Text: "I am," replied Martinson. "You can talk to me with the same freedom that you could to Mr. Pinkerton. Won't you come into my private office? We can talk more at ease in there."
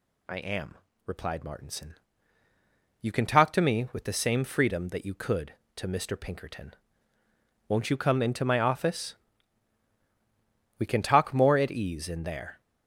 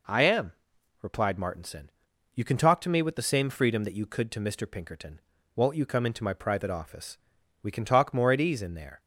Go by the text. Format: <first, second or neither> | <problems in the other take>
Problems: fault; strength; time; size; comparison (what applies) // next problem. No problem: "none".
second | skips "private"; at 8.6 s